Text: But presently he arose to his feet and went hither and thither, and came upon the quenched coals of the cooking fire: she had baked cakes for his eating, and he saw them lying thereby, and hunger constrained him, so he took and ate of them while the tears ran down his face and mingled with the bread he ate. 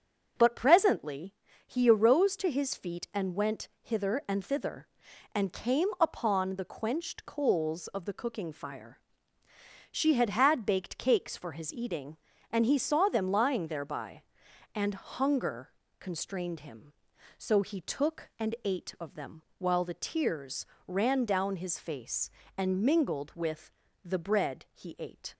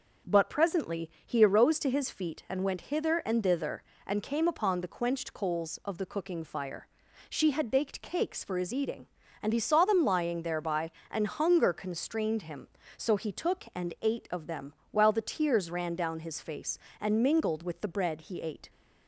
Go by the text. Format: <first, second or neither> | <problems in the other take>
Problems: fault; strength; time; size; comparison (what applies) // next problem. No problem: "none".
second | starts louder than the rest; noticeable; until 1.6 s; 6 dB // pauses between "presently" and "he"; slight; at 1.3 s; 0.32 s long; slight in the second // says "had" twice; at 10.2 s // pauses between "hunger" and "constrained"; slight; at 15.7 s; 0.28 s long // pauses between "them" and "while"; slight; at 19.4 s; 0.16 s long; slight in the second // pauses between "tears" and "ran"; slight; at 20.6 s; 0.20 s long // pauses between "with" and "the"; slight; at 23.7 s; 0.34 s long